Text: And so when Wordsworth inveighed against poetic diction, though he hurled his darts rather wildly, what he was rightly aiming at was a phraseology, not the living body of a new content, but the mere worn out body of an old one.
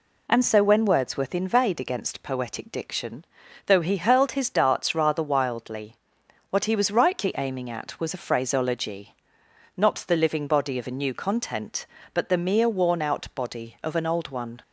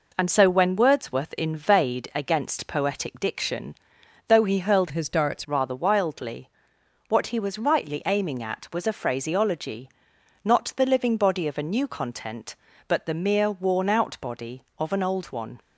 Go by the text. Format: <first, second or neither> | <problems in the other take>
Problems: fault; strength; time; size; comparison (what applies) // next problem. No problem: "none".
first | changes voice from "his" to "darts"; from 4.9 to 5.4 s; 0.5 s long